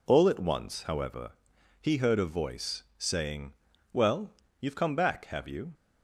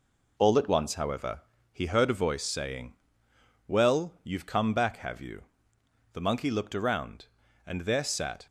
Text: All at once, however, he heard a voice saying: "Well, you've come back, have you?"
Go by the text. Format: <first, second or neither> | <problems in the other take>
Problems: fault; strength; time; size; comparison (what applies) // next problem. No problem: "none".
first | goes on to say "The Monkey looked around and there sat"; strong; from 6.1 s on; 2.3 s long